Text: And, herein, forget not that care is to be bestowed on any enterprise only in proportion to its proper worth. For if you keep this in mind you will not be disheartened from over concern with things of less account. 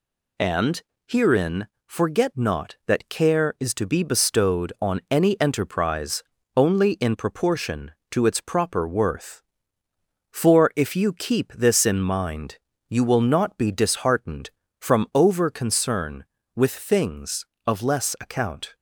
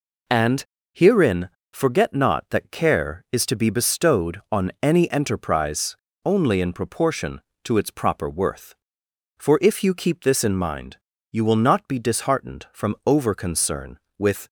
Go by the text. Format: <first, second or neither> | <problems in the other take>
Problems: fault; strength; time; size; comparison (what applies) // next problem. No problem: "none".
first | pauses between "enterprise" and "only"; slight; at 5.9 s; 0.28 s long; slight in the first // pauses between "mind" and "you"; slight; at 10.9 s; 0.36 s long; slight in the first // stops before "things of less account"; at 14.4 s